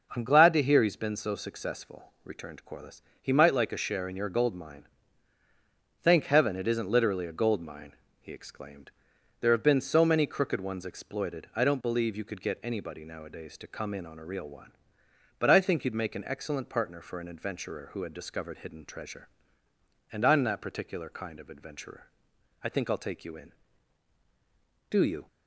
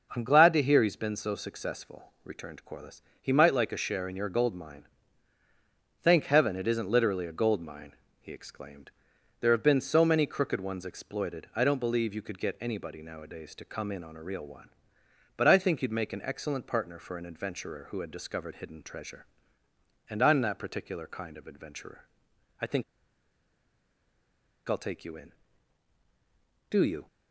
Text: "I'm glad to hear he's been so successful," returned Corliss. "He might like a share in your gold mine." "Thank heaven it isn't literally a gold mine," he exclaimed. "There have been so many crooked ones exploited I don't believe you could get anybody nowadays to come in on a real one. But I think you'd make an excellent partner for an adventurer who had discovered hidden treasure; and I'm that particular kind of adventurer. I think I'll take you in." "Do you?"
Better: first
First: none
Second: pauses between "think" and "I'll"; strong; at 22.8 s; 1.8 s long

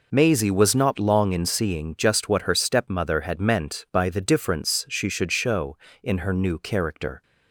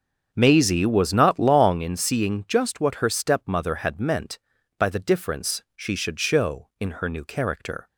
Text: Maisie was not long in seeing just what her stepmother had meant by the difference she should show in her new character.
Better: first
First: none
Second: starts louder than the rest; strong; until 1.9 s; 7 dB

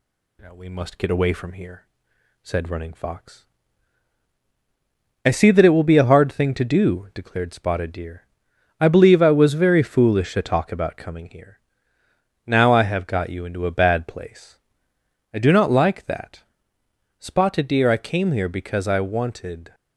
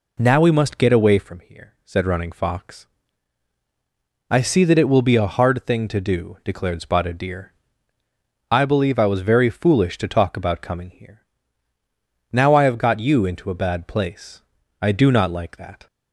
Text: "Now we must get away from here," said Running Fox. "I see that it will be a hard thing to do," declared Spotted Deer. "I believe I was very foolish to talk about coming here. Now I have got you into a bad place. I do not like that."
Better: second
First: goes on to say "Spotted Deer I came here because I wanted"; strong; from 17.1 s on; 2.5 s long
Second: none

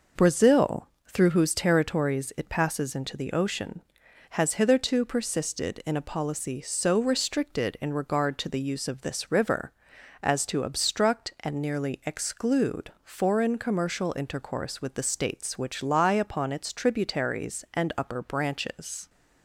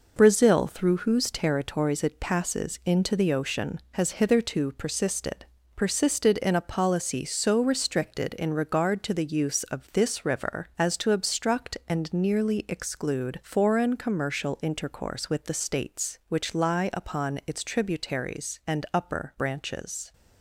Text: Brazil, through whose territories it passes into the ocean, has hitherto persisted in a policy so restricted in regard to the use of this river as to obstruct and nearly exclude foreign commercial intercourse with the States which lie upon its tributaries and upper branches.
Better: first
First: none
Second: says "persisted" twice; at 5.7 s

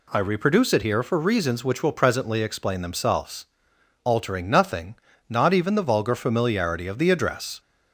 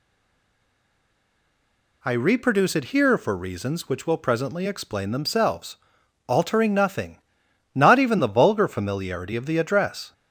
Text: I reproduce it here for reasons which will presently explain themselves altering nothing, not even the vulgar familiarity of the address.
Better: first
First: pauses between "themselves" and "altering"; noticeable; at 3.4 s; 0.58 s long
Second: stays silent before the first word; noticeable; until 2.0 s; 2.0 s long // pauses between "themselves" and "altering"; noticeable; at 5.7 s; 0.52 s long

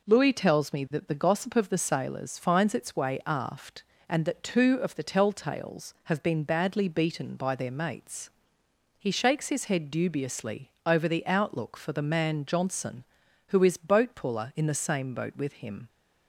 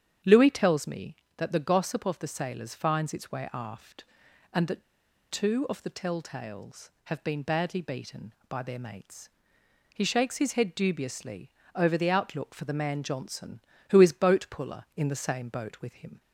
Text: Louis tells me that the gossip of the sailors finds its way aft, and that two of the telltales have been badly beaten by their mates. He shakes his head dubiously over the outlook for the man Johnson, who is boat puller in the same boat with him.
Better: first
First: pauses between "dubiously" and "over"; slight; at 10.6 s; 0.16 s long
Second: starts louder than the rest; strong; until 1.4 s; 9 dB // pauses between "that" and "two"; noticeable; at 4.8 s; 0.47 s long // pauses between "dubiously" and "over"; slight; at 11.4 s; 0.24 s long

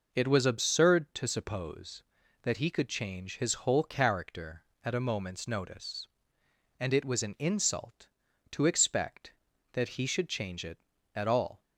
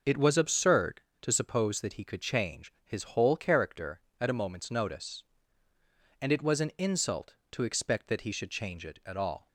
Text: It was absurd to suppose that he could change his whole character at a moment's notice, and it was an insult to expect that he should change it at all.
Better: neither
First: none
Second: none

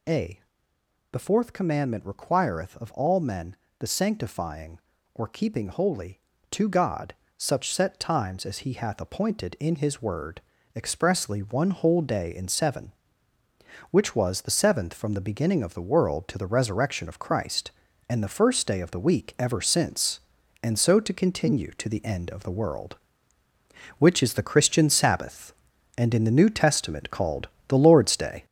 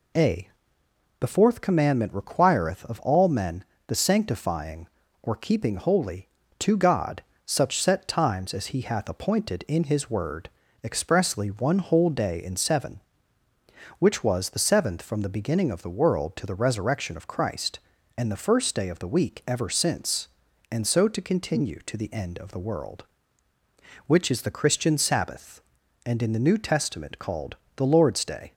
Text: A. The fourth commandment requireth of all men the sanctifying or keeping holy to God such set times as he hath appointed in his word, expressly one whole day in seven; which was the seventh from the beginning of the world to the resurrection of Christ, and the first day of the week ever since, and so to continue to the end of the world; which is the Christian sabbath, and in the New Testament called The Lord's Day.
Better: second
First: gets louder; throughout; 6.5 dB // pauses between "men" and "the"; slight; at 3.5 s; 0.24 s long // pauses between "God" and "such"; slight; at 7.1 s; 0.22 s long // pauses between "called" and "The"; slight; at 27.4 s; 0.18 s long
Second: pauses between "men" and "the"; slight; at 3.6 s; 0.24 s long // pauses between "God" and "such"; slight; at 7.2 s; 0.22 s long // pauses between "called" and "The"; slight; at 27.5 s; 0.18 s long

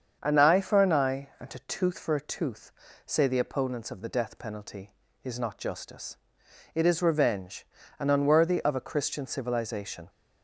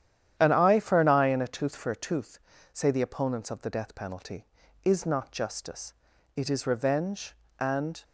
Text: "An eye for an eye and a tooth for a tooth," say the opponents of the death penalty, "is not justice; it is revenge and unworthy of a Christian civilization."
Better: first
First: starts louder than the rest; strong; until 1.2 s; 7 dB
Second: starts louder than the rest; strong; until 1.3 s; 10.5 dB // stops before "unworthy of a Christian civilization"; at 8.0 s

